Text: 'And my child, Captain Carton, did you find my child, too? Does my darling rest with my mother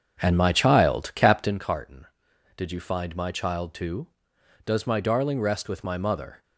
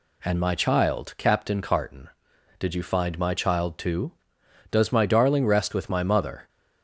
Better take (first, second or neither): second